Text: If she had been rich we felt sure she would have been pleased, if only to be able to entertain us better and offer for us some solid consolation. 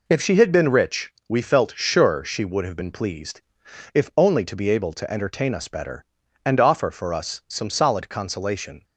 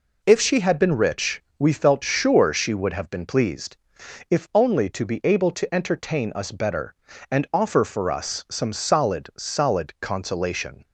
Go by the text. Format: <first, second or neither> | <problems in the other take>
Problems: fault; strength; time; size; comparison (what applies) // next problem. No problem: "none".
first | pauses between "rich" and "we"; slight; at 1.4 s; 0.16 s long; slight in the first // says "solid" twice; at 9.3 s